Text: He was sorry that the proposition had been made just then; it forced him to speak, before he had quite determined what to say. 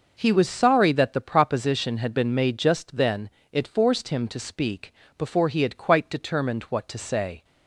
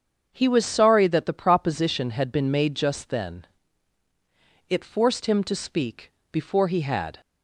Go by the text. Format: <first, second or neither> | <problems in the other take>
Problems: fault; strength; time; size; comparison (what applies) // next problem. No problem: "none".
first | starts louder than the rest; until 1.3 s; 7 dB // stops before "quite determined what to say"; at 7.2 s